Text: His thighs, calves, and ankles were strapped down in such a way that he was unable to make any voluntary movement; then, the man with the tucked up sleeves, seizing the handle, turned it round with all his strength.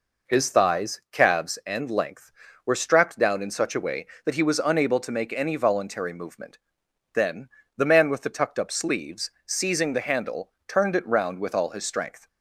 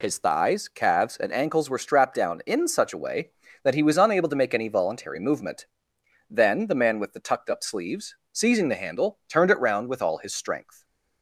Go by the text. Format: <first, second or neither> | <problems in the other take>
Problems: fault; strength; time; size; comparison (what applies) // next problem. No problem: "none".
second | says "length" for "ankles"; at 1.8 s